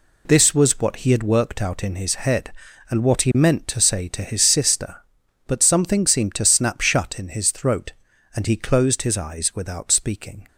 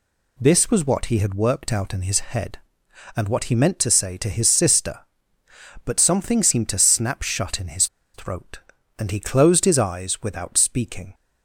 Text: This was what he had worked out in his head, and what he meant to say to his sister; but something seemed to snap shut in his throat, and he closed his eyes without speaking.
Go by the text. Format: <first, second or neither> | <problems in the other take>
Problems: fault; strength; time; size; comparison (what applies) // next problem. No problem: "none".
first | pauses between "his" and "throat"; slight; at 7.8 s; 0.27 s long